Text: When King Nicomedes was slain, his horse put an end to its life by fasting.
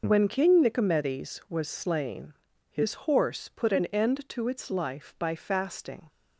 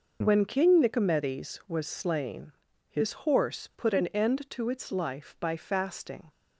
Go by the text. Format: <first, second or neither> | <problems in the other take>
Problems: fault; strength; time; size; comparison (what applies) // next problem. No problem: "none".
neither | none